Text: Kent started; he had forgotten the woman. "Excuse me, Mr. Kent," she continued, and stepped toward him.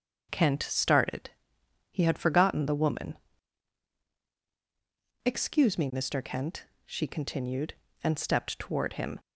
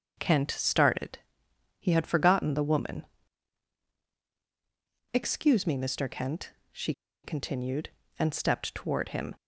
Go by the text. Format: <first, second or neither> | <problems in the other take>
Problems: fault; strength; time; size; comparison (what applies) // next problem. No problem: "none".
first | starts louder than the rest; until 1.1 s; 6.5 dB; also in the first // pauses between "she" and "continued"; slight; at 6.9 s; 0.31 s long